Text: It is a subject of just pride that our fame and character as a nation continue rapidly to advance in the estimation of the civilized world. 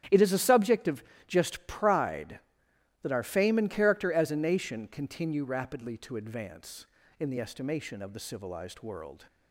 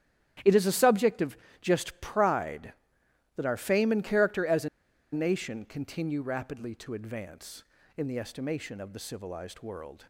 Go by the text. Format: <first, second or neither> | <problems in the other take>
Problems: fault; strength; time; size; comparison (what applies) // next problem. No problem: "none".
first | starts louder than the rest; strong; until 1.6 s; 10.5 dB; strong in the first // pauses between "of" and "just"; slight; at 1.3 s; 0.24 s long; slight in the first // pauses between "a" and "nation"; at 4.6 s; 0.45 s long